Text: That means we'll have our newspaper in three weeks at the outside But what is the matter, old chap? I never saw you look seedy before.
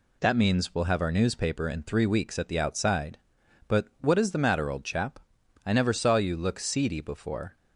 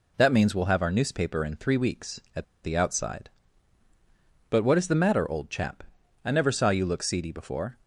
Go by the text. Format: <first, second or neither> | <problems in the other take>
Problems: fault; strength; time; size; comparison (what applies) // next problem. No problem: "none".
first | pauses between "at" and "the"; slight; at 2.4 s; 0.18 s long